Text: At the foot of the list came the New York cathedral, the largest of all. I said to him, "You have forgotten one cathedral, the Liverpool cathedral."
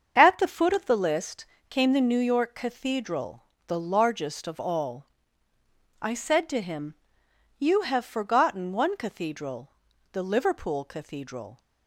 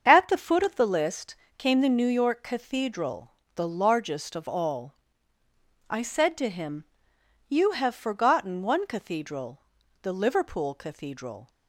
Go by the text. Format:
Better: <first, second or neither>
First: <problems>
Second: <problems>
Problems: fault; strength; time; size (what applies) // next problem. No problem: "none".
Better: neither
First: starts louder than the rest; until 1.1 s; 7 dB // pauses between "list" and "came"; slight; at 1.4 s; 0.24 s long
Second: starts louder than the rest; until 1.0 s; 7 dB // pauses between "list" and "came"; slight; at 1.3 s; 0.22 s long